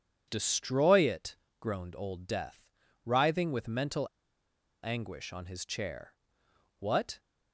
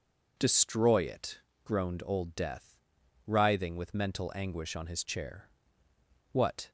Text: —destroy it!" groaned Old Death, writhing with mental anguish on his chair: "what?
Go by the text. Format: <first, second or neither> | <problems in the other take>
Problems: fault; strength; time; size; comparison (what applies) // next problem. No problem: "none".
second | pauses between "mental" and "anguish"; noticeable; at 4.0 s; 0.80 s long